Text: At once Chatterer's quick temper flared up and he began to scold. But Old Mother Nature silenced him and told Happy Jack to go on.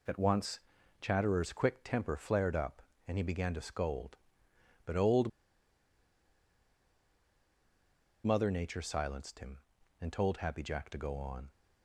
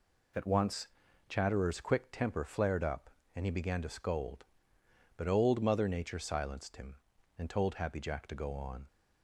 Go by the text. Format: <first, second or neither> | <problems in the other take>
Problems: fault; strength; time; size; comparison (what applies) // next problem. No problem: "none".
second | pauses between "once" and "Chatterer's"; at 0.6 s; 0.40 s long; also in the second // pauses between "Old" and "Mother"; strong; at 5.2 s; 2.9 s long